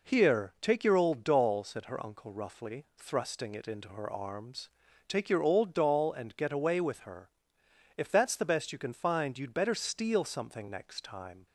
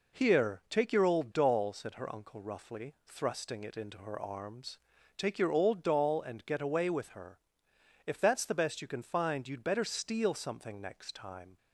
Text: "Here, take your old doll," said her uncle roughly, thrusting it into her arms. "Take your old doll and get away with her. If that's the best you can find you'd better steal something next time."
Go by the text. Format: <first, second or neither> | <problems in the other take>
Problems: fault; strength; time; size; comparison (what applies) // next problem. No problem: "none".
neither | none